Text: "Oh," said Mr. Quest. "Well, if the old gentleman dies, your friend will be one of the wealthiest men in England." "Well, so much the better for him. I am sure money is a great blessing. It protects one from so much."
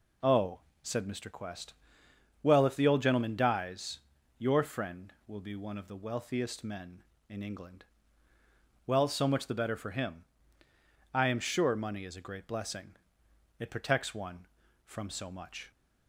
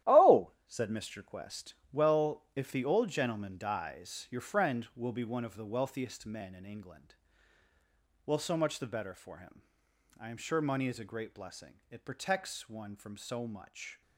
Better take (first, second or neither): first